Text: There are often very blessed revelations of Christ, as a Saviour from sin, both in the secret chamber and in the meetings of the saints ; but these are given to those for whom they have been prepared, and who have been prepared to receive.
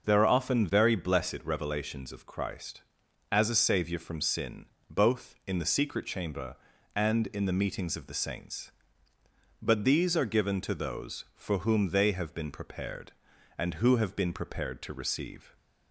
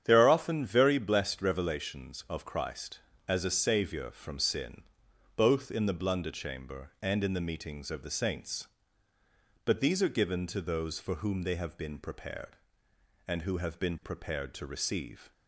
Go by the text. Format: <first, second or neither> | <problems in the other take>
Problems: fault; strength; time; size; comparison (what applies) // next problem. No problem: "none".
first | starts louder than the rest; strong; until 1.0 s; 9 dB; also in the first // says "blunder" for "secret"; at 5.9 s